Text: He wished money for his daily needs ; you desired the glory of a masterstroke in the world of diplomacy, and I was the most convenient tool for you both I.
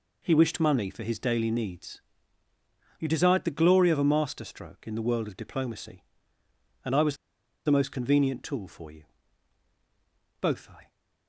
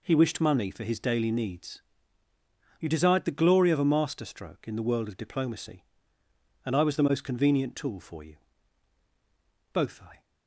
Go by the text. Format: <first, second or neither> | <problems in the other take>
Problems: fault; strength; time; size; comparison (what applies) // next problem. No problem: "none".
second | pauses between "was" and "the"; noticeable; at 7.1 s; 0.49 s long // pauses between "you" and "both"; strong; at 9.0 s; 1.3 s long; strong in the second